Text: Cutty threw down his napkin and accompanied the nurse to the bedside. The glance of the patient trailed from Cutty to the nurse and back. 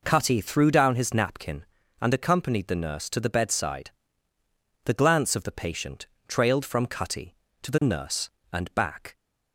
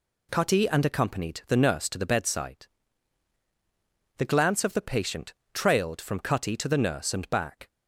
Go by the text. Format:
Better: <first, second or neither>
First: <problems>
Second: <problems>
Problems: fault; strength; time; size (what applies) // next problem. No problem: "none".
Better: first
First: pauses between "patient" and "trailed"; slight; at 6.0 s; 0.22 s long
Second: skips "threw down his napkin"; at 0.6 s // pauses between "patient" and "trailed"; slight; at 5.3 s; 0.22 s long